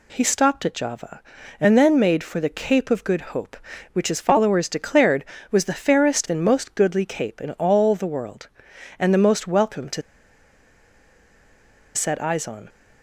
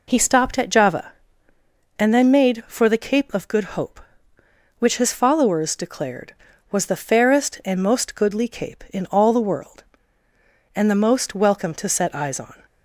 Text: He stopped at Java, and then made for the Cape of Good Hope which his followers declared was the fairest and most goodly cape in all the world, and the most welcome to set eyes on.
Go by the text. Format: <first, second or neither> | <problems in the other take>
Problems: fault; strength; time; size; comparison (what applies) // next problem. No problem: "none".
second | pauses between "to" and "set"; strong; at 10.0 s; 1.9 s long